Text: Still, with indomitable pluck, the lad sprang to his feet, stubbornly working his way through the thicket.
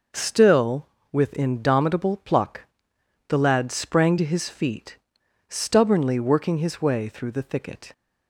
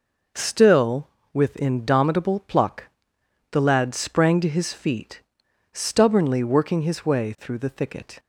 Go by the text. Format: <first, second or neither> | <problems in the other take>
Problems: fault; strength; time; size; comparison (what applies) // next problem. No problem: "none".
neither | none